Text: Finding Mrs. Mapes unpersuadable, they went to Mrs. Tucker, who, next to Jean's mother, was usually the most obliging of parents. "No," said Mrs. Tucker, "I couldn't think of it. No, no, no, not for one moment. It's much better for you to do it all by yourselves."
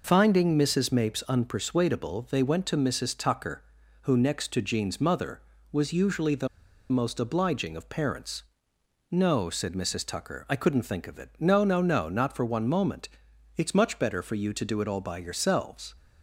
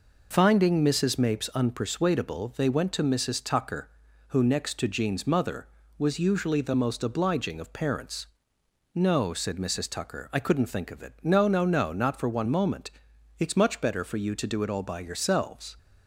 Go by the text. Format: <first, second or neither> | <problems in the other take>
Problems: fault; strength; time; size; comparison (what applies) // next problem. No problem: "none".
second | pauses between "the" and "most"; at 6.4 s; 0.42 s long